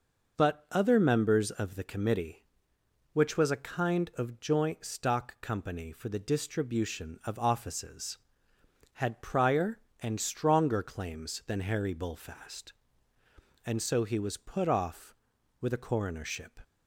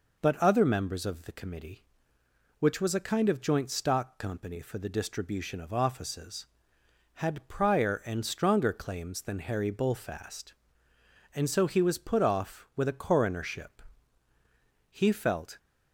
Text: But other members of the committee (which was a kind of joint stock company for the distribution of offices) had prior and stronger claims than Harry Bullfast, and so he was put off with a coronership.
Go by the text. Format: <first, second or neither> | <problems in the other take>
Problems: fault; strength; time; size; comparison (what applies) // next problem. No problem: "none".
first | goes on to say "He felt"; noticeable; from 14.8 s on; 0.68 s long